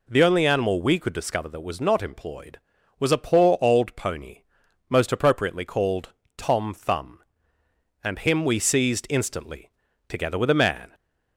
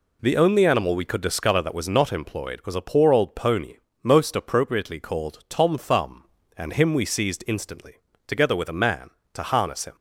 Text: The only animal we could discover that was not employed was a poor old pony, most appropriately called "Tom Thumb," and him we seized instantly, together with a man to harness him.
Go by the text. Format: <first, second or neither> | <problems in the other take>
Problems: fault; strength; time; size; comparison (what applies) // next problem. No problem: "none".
second | pauses between "called" and "Tom"; slight; at 6.1 s; 0.24 s long // stops before "to harness him"; at 10.9 s